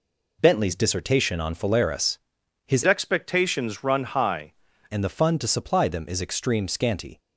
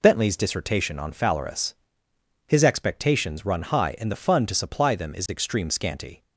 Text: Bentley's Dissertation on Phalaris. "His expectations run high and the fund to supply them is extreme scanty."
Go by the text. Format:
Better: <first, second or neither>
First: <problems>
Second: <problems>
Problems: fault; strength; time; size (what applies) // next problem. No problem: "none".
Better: second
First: changes voice from "expectations" to "high"; from 2.8 to 4.5 s; 1.7 s long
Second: none